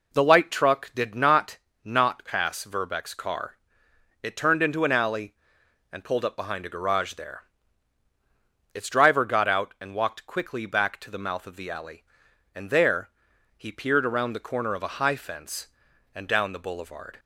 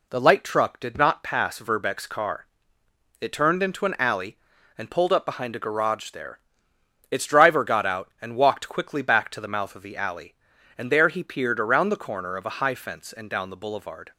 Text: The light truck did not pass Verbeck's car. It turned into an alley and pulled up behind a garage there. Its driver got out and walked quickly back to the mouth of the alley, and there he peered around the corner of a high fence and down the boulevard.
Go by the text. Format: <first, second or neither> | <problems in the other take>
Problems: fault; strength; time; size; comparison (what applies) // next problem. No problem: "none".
second | says "not" twice; at 1.8 s // pauses between "there" and "he"; noticeable; at 13.0 s; 0.48 s long